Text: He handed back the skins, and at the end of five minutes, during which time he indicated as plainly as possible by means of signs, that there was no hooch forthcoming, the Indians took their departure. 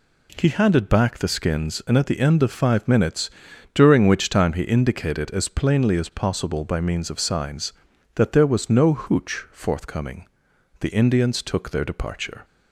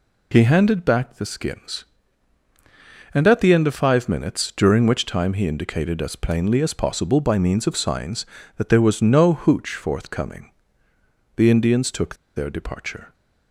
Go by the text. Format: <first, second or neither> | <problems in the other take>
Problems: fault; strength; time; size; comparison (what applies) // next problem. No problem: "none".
first | pauses between "took" and "their"; slight; at 12.1 s; 0.21 s long